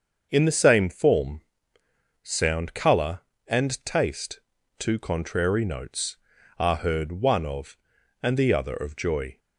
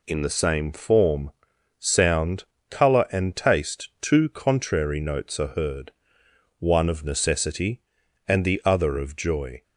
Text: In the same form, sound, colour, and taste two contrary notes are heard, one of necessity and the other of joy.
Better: second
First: starts louder than the rest; until 1.3 s; 6.5 dB // pauses between "taste" and "two"; at 4.4 s; 0.38 s long // skips "necessity"; at 7.9 s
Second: none

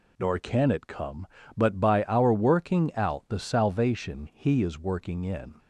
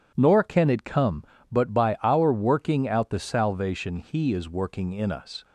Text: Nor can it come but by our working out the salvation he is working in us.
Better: second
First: stops before "us"; at 5.5 s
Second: none

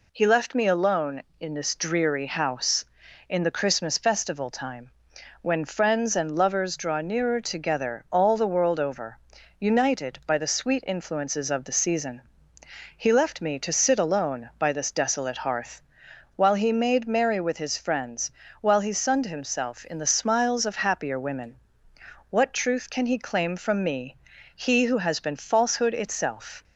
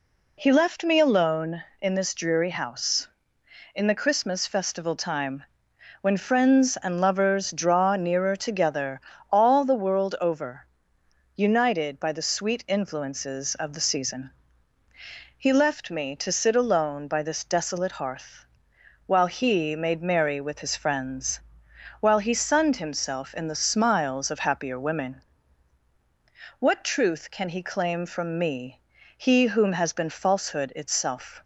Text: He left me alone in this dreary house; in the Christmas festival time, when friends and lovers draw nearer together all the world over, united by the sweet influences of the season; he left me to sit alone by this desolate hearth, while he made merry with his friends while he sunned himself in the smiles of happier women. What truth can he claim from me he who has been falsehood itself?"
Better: first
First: pauses between "friends" and "while"; slight; at 18.3 s; 0.30 s long // pauses between "me" and "he"; at 24.1 s; 0.40 s long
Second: pauses between "together" and "all"; slight; at 9.0 s; 0.32 s long // pauses between "friends" and "while"; noticeable; at 21.4 s; 0.58 s long // pauses between "me" and "he"; at 28.7 s; 0.42 s long // says "whom" for "who"; at 29.4 s

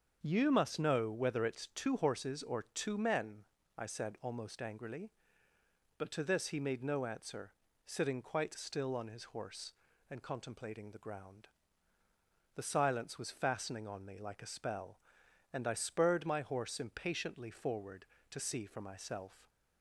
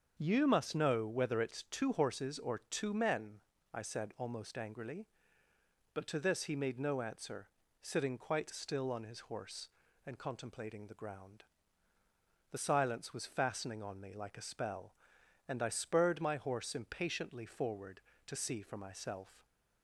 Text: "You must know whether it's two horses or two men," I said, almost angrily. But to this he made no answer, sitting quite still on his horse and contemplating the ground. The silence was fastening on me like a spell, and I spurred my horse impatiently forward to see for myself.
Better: neither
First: starts louder than the rest; until 1.2 s; 7 dB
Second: starts louder than the rest; until 1.1 s; 7 dB

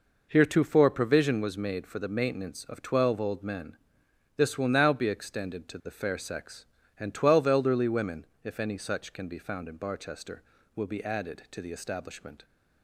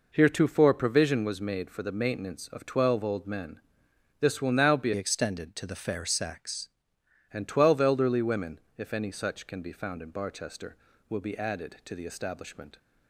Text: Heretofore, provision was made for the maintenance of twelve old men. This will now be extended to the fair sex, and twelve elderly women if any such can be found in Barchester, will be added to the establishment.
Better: first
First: pauses between "women" and "if"; slight; at 8.2 s; 0.16 s long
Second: changes voice from "extended" to "sex"; from 4.9 to 6.6 s; 1.7 s long // pauses between "women" and "if"; slight; at 8.5 s; 0.16 s long

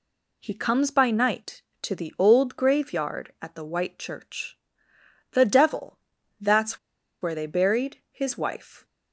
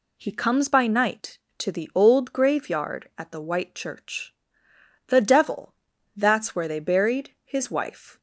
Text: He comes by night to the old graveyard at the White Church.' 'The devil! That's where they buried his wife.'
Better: second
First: pauses between "That's" and "where"; at 6.7 s; 0.43 s long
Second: none

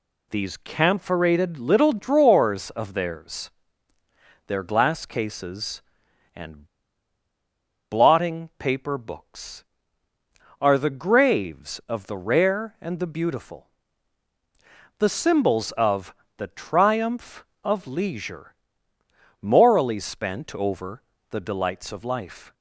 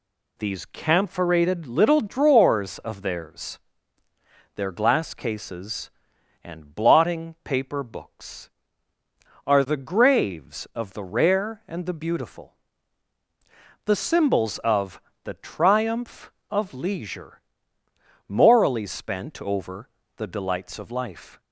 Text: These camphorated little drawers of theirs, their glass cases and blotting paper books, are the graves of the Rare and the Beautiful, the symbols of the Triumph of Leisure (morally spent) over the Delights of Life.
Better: second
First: pauses between "and" and "blotting"; at 6.6 s; 1.2 s long // pauses between "of" and "the"; slight; at 16.1 s; 0.24 s long // pauses between "over" and "the"; slight; at 21.0 s; 0.30 s long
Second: pauses between "of" and "the"; slight; at 14.9 s; 0.24 s long // pauses between "over" and "the"; slight; at 19.8 s; 0.30 s long

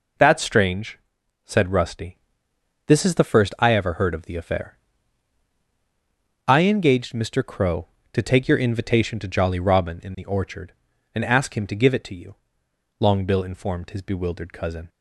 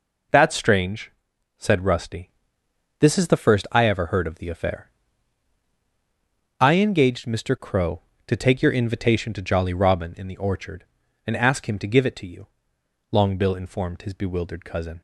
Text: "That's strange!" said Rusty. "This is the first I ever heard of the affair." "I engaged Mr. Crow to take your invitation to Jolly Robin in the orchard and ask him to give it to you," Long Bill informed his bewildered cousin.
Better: neither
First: none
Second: none

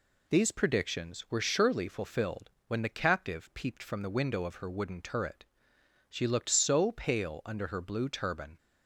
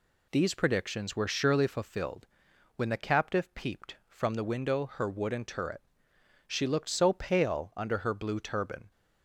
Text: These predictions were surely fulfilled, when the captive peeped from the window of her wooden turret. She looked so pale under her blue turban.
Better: first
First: none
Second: skips "of"; at 4.8 s

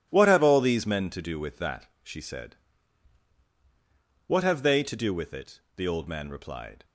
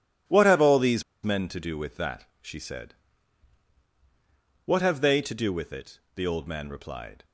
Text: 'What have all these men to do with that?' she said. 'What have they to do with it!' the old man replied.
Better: first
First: none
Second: pauses between "these" and "men"; slight; at 1.0 s; 0.21 s long

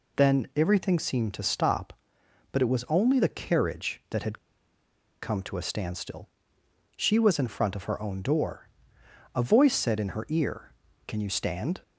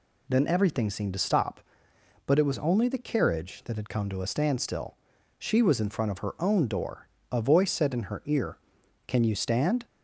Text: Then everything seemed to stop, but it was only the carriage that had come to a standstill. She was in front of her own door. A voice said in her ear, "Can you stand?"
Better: second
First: pauses between "had" and "come"; noticeable; at 4.3 s; 0.83 s long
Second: none

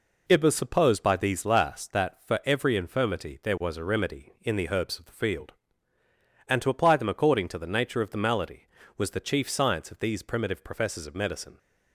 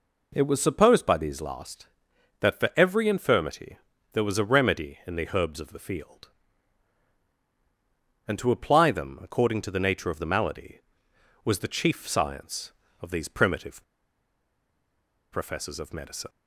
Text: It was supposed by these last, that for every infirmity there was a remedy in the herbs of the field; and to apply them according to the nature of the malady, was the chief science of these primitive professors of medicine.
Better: first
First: none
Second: pauses between "infirmity" and "there"; slight; at 3.7 s; 0.36 s long // pauses between "primitive" and "professors"; strong; at 13.8 s; 1.4 s long

